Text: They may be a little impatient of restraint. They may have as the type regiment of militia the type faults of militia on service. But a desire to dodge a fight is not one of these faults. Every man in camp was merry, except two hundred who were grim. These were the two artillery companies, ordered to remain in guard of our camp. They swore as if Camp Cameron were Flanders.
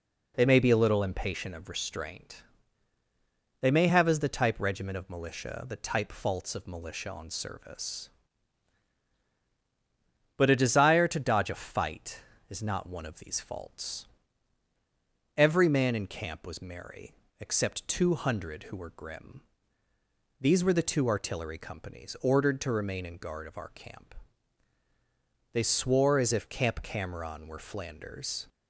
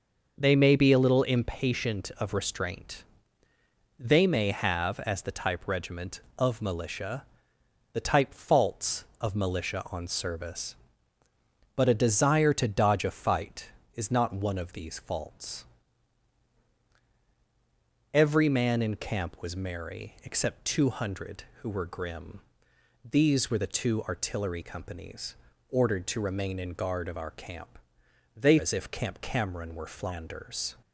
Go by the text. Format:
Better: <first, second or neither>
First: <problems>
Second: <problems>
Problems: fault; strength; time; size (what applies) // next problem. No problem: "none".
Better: first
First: none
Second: pauses between "militia" and "the"; noticeable; at 7.2 s; 0.70 s long // skips "swore"; at 28.5 s